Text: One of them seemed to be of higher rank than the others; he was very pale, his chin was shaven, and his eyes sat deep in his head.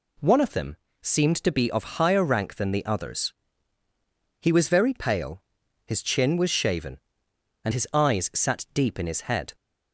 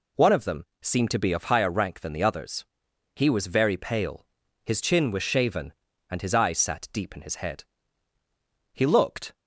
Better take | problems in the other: first | pauses between "them" and "seemed"; slight; at 0.6 s; 0.16 s long; slight in the first // goes on to say "He looked"; noticeable; from 8.7 s on; 0.62 s long

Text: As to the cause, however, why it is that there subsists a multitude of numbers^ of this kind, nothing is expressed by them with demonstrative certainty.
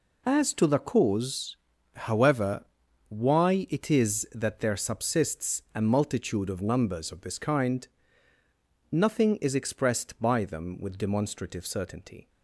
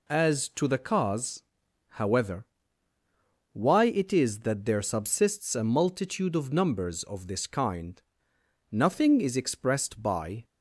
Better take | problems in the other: first | stops before "them with demonstrative certainty"; at 10.4 s

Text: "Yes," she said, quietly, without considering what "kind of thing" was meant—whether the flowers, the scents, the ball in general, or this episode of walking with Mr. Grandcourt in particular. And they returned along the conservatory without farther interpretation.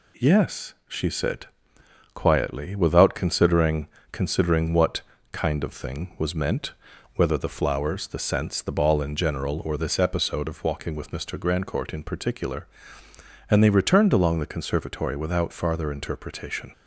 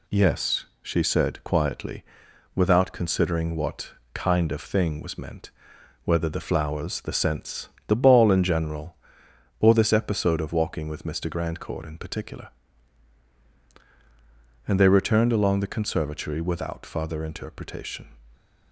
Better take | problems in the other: second | says "considering" twice; at 4.1 s // pauses between "what" and "kind"; slight; at 5.0 s; 0.30 s long; slight in the second

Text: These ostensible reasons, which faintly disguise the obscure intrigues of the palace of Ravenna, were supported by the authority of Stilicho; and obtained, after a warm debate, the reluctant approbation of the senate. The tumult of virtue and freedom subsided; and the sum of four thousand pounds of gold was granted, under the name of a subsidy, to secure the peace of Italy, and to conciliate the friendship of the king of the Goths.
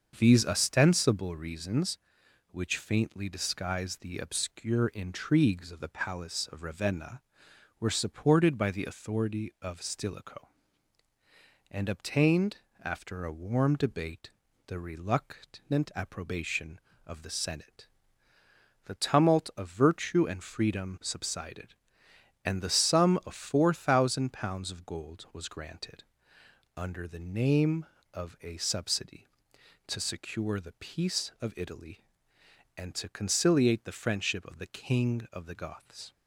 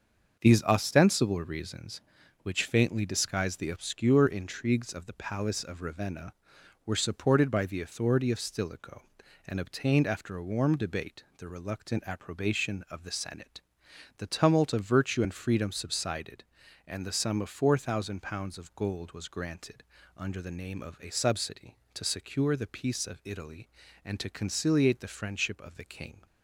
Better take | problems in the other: first | starts louder than the rest; until 1.4 s; 6.5 dB; also in the first // stops before "of the Goths"; at 26.2 s

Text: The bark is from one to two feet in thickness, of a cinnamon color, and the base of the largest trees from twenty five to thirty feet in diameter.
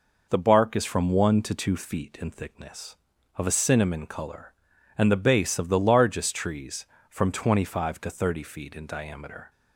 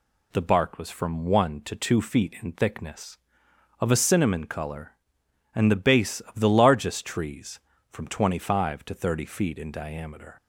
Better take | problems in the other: first | says "was" for "is"; at 0.7 s

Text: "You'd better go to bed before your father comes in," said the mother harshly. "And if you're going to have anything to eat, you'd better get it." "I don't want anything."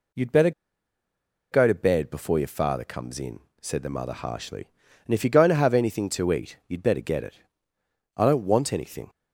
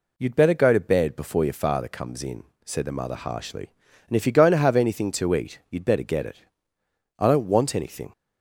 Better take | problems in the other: second | pauses between "better" and "go"; at 0.5 s; 1.0 s long

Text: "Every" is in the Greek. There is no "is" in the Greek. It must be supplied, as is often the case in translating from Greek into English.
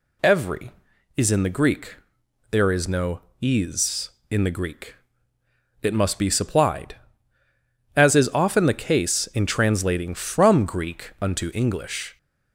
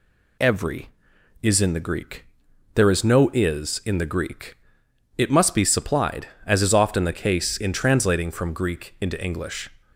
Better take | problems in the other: second | says "unto" for "into"; at 11.2 s

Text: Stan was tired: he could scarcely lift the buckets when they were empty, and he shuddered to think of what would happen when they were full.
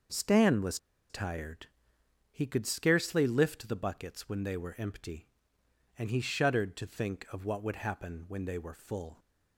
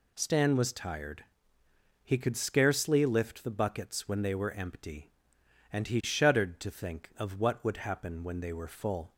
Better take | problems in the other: second | pauses between "was" and "tired"; slight; at 0.7 s; 0.32 s long

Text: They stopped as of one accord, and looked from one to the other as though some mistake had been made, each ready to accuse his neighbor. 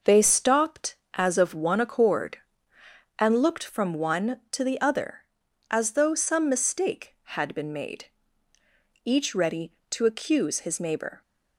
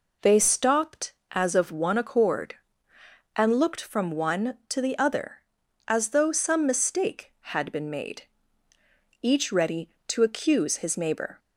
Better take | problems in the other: second | gets quieter; noticeable; throughout; 6 dB

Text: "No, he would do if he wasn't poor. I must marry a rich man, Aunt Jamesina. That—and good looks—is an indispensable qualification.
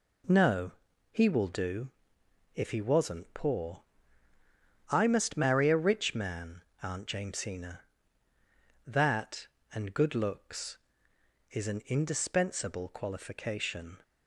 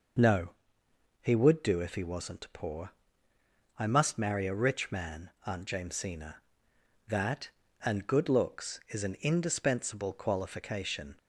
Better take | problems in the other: second | says "will" for "would"; at 1.2 s // pauses between "do" and "if"; noticeable; at 1.9 s; 0.64 s long

